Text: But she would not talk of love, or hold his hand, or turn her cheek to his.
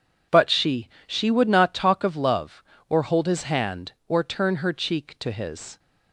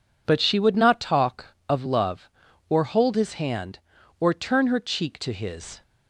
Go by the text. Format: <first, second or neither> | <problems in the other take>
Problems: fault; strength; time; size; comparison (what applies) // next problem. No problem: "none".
second | says "she" twice; at 1.0 s